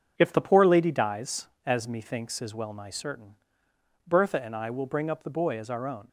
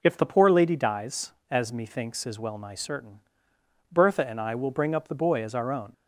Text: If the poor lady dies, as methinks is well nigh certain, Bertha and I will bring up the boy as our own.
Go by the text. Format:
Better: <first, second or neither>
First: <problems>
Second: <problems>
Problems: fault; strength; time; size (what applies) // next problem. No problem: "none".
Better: second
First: gets quieter; noticeable; throughout; 5.5 dB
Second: none